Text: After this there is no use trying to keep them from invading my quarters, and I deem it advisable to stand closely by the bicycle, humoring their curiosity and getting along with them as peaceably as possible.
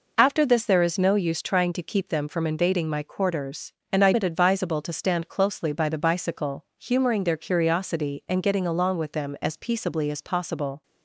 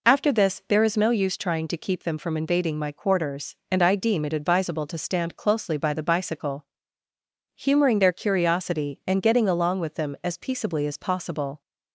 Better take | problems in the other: second | skips "deem"; at 4.1 s

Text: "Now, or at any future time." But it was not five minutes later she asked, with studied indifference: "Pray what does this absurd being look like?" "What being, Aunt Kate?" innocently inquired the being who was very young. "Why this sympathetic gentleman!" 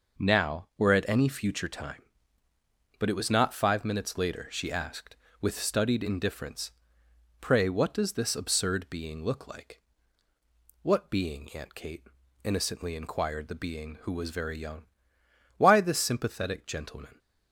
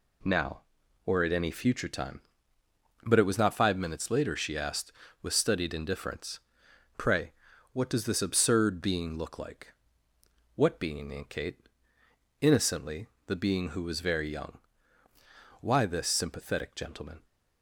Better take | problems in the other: first | pauses between "Pray" and "what"; at 7.3 s; 0.40 s long // skips "inquired"; at 13.1 s

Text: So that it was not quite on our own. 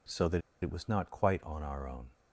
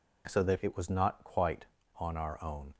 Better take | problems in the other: second | pauses between "that" and "it"; slight; at 0.4 s; 0.21 s long

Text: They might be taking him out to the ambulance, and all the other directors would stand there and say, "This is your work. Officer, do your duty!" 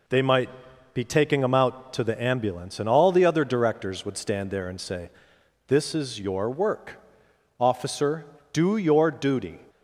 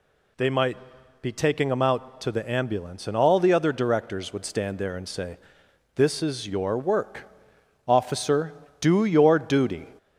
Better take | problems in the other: first | gets louder; slight; throughout; 2.5 dB // pauses between "might" and "be"; noticeable; at 0.7 s; 0.46 s long; noticeable in the first

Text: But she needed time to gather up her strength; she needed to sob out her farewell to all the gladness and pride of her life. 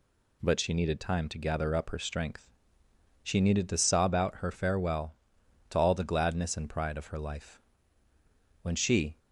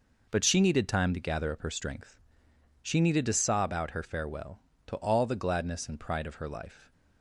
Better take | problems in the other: second | goes on to say "When she"; from 8.6 s on; 0.56 s long

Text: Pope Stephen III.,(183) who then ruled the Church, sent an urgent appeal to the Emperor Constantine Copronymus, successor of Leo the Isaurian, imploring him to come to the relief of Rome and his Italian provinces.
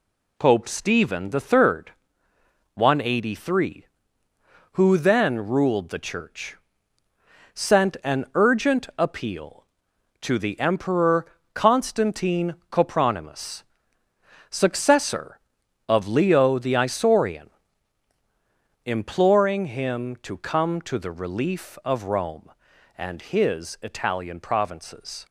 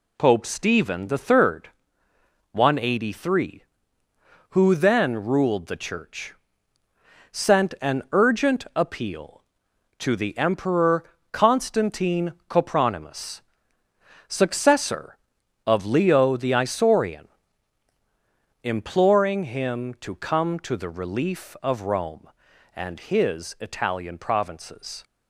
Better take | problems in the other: neither | pauses between "Emperor" and "Constantine"; slight; the same in both

